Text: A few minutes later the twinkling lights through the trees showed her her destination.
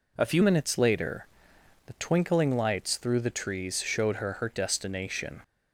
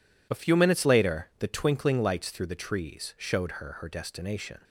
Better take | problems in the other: second | changes voice at "minutes"; from 0.4 s on; 5.0 s long // pauses between "later" and "the"; noticeable; at 1.2 s; 0.60 s long

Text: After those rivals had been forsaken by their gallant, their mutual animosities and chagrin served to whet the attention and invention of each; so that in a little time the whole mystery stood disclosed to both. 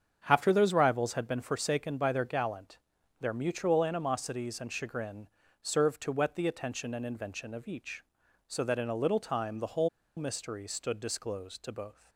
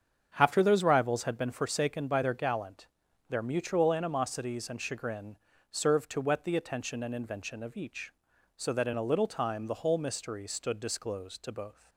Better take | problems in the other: second | starts louder than the rest; strong; until 1.2 s; 7.5 dB; strong in the second // pauses between "chagrin" and "served"; slight; at 5.2 s; 0.34 s long; slight in the second // pauses between "whole" and "mystery"; slight; at 9.8 s; 0.28 s long

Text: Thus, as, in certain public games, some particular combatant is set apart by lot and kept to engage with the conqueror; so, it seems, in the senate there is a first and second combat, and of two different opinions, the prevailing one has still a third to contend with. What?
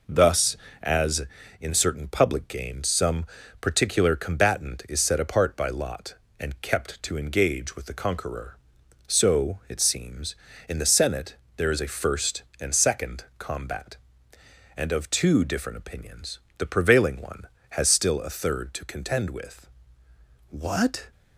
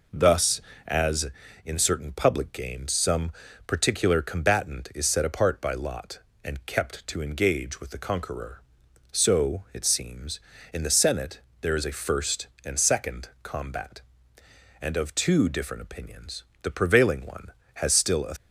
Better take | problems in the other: first | pauses between "some" and "particular"; slight; at 3.3 s; 0.36 s long; slight in the first // pauses between "senate" and "there"; slight; at 11.4 s; 0.18 s long; slight in the first // pauses between "second" and "combat"; slight; at 13.2 s; 0.16 s long; slight in the first // stops before "third to contend with What"; at 18.3 s

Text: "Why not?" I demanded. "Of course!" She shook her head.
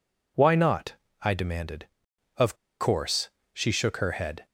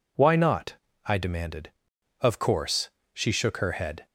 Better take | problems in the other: second | pauses between "Of" and "course"; slight; at 2.5 s; 0.24 s long

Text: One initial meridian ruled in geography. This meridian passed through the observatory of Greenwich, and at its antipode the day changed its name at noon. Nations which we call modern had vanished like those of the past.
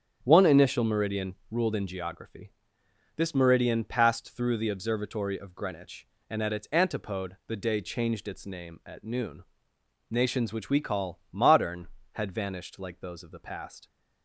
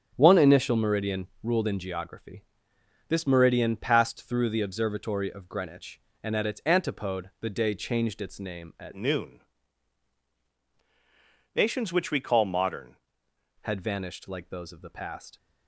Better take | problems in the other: first | starts louder than the rest; strong; until 1.1 s; 7.5 dB; strong in the first // changes voice from "noon" to "modern"; from 8.9 to 12.9 s; 4.0 s long

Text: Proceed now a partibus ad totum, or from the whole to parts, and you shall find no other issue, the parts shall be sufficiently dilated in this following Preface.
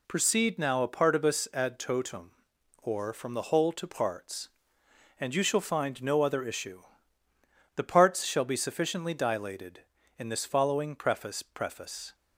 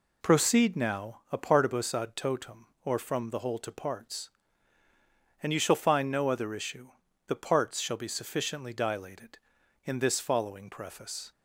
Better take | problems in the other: second | says "Preface" twice; at 11.4 s

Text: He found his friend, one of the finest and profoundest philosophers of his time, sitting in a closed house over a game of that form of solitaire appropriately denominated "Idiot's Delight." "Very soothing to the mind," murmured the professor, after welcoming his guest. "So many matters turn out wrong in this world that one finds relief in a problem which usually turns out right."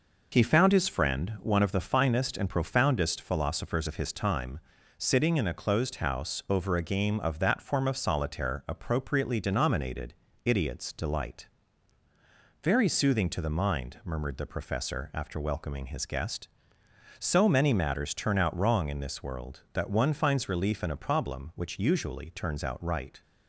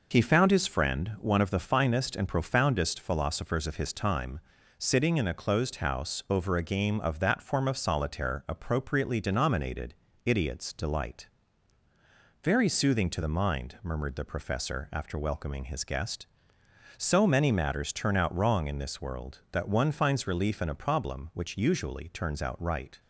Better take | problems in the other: neither | pauses between "denominated" and "Idiot's"; slight; the same in both

